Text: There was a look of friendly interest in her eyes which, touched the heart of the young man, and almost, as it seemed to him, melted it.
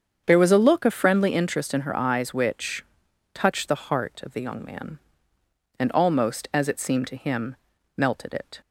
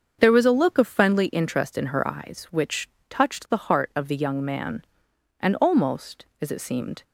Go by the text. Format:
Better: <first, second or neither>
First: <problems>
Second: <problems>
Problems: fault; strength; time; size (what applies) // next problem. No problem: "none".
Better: first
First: starts louder than the rest; strong; until 1.2 s; 7.5 dB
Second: starts louder than the rest; until 1.2 s; 6.5 dB // stops before "to him melted it"; at 7.0 s